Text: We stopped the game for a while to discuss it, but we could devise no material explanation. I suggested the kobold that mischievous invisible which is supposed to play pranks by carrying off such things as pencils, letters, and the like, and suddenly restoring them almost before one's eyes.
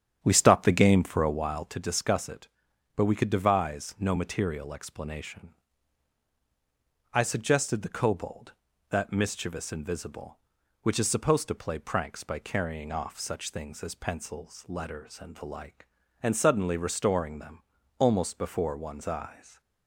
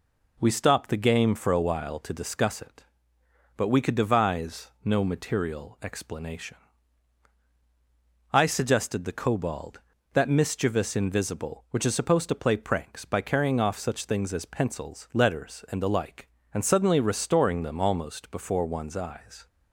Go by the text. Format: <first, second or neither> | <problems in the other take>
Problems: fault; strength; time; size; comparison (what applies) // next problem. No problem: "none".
second | starts louder than the rest; strong; until 1.8 s; 9 dB // pauses between "them" and "almost"; at 17.6 s; 0.37 s long